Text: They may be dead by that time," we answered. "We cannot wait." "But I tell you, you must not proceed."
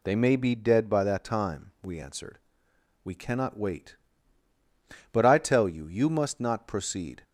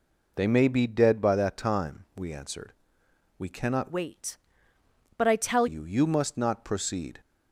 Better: first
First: none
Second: changes voice from "wait" to "tell"; from 3.8 to 5.6 s; 1.8 s long

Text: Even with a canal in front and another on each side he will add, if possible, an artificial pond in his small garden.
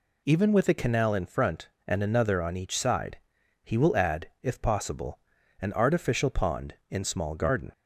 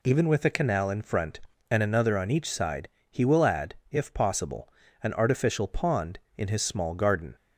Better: second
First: pauses between "side" and "he"; at 3.1 s; 0.44 s long // skips "his"; at 7.0 s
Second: pauses between "side" and "he"; slight; at 2.8 s; 0.24 s long

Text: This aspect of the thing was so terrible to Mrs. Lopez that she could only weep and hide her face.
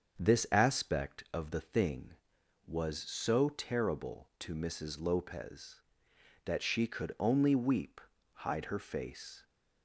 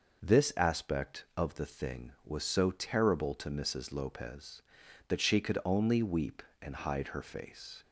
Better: second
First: starts louder than the rest; until 1.2 s; 7 dB // skips "and"; at 8.1 s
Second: none

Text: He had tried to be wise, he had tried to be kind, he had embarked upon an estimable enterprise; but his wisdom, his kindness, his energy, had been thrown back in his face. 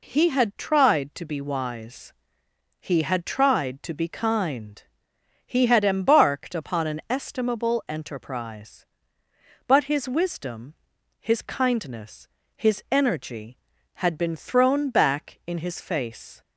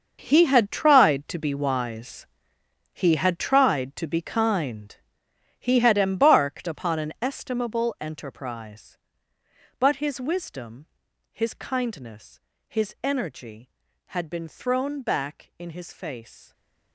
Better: first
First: none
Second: gets quieter; strong; throughout; 14.5 dB

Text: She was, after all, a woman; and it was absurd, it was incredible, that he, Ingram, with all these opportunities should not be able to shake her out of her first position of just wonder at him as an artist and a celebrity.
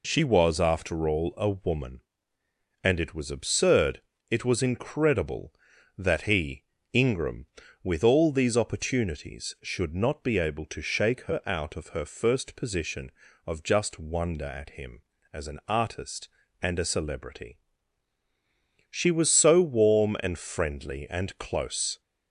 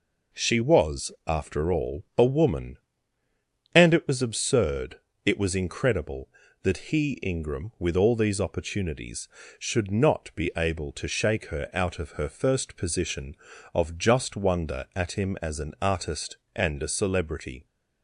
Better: second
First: goes on to say "She was so warm and friendly and close"; strong; from 18.9 s on; 3.1 s long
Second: none

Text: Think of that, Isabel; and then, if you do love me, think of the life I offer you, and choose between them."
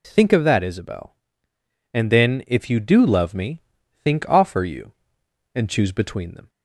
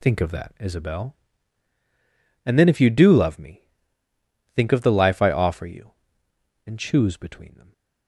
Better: second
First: skips "of the life I"; at 4.2 s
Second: none

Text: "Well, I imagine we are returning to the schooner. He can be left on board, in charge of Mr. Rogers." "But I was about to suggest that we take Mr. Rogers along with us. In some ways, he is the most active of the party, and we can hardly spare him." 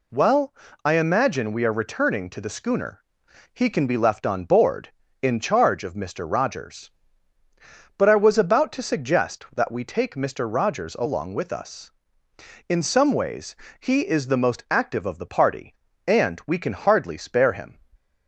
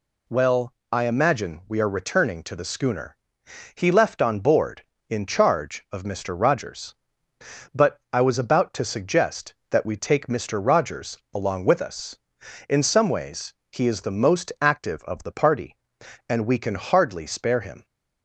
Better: first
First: none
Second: skips "can be"; at 3.9 s // pauses between "Rogers" and "along"; slight; at 11.1 s; 0.16 s long

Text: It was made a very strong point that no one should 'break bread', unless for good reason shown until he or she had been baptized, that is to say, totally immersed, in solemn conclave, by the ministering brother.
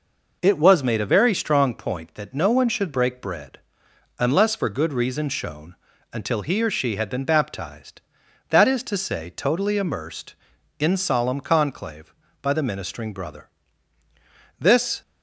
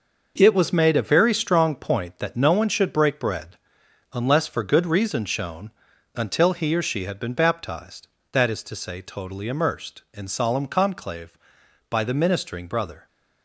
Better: second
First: pauses between "shown" and "until"; at 5.7 s; 0.38 s long // goes on to say "This"; slight; from 14.5 s on; 0.42 s long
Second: pauses between "shown" and "until"; at 5.7 s; 0.44 s long

